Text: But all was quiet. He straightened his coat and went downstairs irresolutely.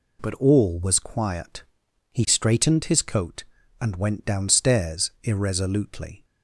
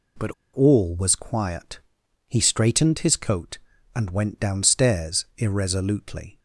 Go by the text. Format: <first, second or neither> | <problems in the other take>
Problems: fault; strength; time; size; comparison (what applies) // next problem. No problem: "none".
first | pauses between "But" and "all"; slight; at 0.3 s; 0.22 s long